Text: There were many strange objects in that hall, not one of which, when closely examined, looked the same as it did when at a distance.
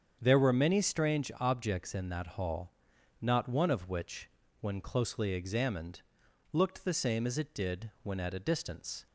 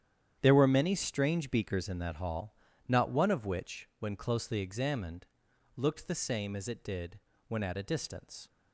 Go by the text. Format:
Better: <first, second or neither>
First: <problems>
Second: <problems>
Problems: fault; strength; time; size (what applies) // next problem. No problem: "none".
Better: first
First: starts louder than the rest; strong; until 1.2 s; 7.5 dB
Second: starts louder than the rest; strong; until 1.4 s; 9.5 dB // says "beakers" for "objects"; at 1.5 s // pauses between "did" and "when"; slight; at 7.1 s; 0.30 s long